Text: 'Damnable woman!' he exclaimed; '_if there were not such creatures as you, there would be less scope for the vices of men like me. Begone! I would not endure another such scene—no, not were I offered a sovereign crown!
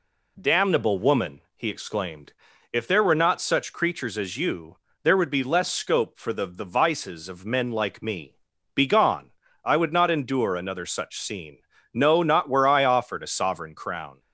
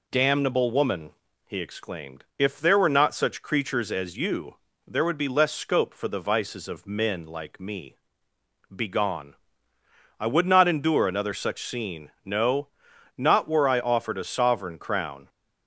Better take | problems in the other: second | says "the" twice; at 6.4 s

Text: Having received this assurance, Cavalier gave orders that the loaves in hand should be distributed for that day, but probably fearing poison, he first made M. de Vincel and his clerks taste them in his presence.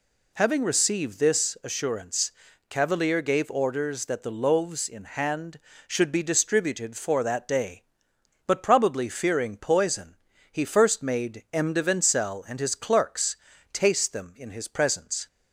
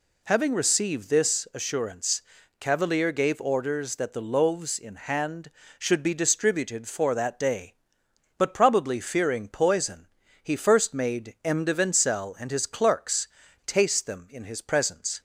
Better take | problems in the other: neither | pauses between "clerks" and "taste"; the same in both

